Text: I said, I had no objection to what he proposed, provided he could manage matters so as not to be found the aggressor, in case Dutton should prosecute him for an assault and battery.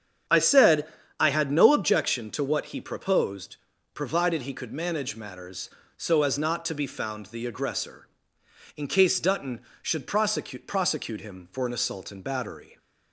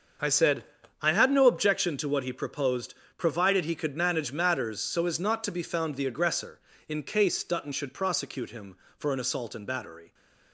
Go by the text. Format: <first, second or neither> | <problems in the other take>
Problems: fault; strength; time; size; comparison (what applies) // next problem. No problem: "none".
second | starts louder than the rest; strong; until 1.6 s; 8 dB; also in the second // says "prosecute" twice; at 10.6 s